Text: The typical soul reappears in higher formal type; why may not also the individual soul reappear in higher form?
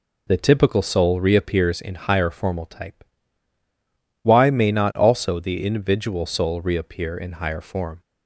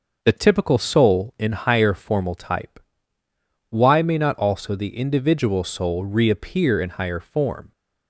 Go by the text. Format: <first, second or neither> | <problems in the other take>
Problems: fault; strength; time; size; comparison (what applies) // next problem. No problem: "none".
first | starts louder than the rest; noticeable; until 1.2 s; 6 dB // skips "reappears"; at 1.3 s